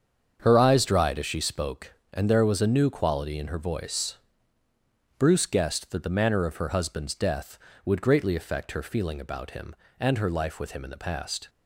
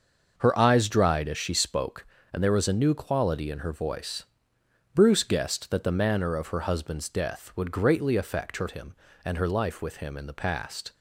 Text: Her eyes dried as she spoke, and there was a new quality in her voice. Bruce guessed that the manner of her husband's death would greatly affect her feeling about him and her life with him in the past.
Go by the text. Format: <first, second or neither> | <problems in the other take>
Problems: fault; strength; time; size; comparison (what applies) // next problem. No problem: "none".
first | starts louder than the rest; noticeable; until 1.3 s; 6 dB; strong in the first // skips "feeling about"; at 8.6 s